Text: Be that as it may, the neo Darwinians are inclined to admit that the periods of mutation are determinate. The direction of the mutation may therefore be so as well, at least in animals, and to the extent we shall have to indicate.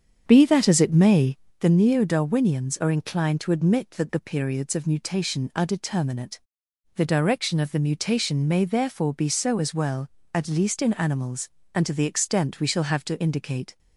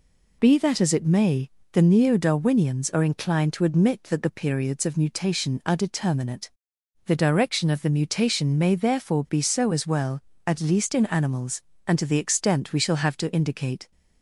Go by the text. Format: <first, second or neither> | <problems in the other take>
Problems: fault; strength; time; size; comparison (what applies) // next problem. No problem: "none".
second | starts louder than the rest; strong; until 1.6 s; 7.5 dB